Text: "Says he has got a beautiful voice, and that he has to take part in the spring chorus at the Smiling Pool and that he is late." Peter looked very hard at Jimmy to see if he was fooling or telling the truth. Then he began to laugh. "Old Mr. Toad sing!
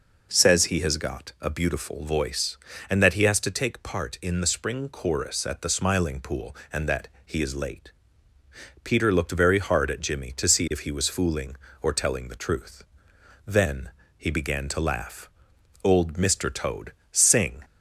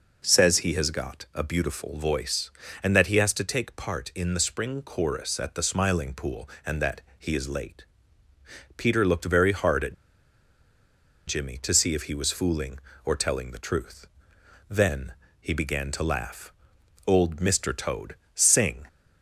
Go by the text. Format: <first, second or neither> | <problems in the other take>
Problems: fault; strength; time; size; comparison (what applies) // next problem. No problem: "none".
first | pauses between "that" and "he"; slight; at 7.0 s; 0.18 s long; slight in the first // pauses between "at" and "Jimmy"; strong; at 9.9 s; 1.3 s long // pauses between "Then" and "he"; slight; at 15.1 s; 0.26 s long; slight in the first // pauses between "Toad" and "sing"; slight; at 18.1 s; 0.18 s long; slight in the first